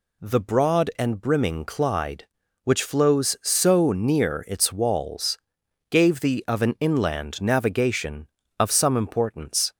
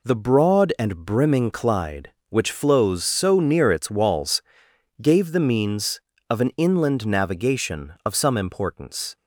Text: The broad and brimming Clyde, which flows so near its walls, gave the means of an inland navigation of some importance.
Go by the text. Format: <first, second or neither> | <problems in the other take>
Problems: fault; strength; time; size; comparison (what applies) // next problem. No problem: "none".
second | skips "means"; at 6.4 s